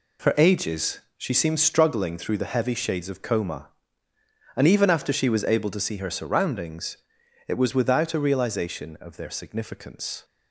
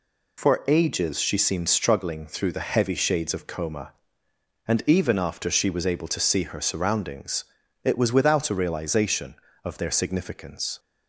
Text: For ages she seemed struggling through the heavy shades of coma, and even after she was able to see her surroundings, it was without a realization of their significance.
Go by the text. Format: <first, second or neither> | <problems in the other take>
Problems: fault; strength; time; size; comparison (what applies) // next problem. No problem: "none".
second | gets quieter; strong; throughout; 8.5 dB // pauses between "ages" and "she"; slight; at 1.0 s; 0.16 s long